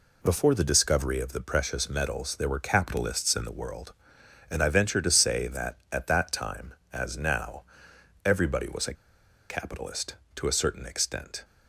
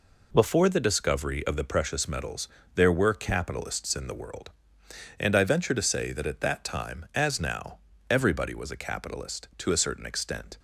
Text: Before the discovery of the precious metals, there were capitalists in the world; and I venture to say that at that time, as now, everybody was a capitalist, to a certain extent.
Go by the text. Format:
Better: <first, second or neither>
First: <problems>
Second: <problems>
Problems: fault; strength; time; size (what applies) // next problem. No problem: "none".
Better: second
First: pauses between "a" and "capitalist"; noticeable; at 8.9 s; 0.57 s long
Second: none